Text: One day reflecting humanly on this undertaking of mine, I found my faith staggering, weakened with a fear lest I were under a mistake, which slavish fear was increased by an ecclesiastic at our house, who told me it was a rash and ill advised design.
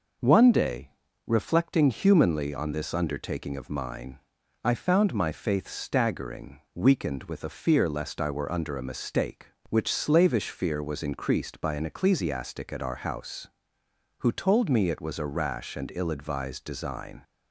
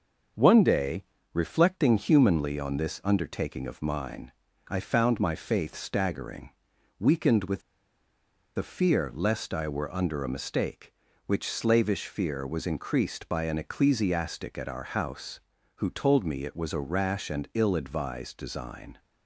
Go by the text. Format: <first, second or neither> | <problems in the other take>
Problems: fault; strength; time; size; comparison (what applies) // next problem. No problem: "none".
first | starts louder than the rest; until 1.6 s; 6.5 dB // pauses between "day" and "reflecting"; slight; at 1.0 s; 0.30 s long; slight in the first // pauses between "with" and "a"; noticeable; at 7.6 s; 0.97 s long